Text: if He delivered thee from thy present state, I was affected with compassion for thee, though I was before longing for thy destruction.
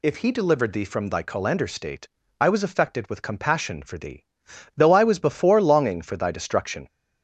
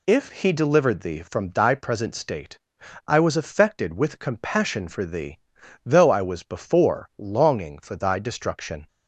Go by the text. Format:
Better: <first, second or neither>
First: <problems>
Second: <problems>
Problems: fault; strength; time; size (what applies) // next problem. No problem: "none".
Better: second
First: says "colander" for "present"; at 1.2 s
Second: none